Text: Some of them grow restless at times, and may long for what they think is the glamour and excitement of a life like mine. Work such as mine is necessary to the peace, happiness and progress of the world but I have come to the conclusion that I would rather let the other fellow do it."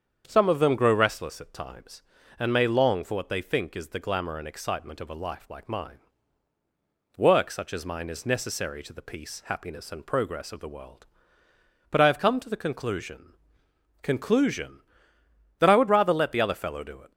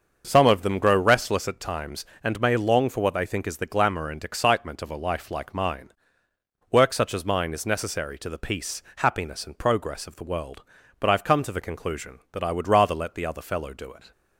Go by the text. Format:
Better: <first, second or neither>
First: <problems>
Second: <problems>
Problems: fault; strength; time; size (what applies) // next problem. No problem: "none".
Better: second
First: starts louder than the rest; strong; until 1.2 s; 7.5 dB // says "conclusion" twice; at 14.0 s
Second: starts louder than the rest; until 1.2 s; 6.5 dB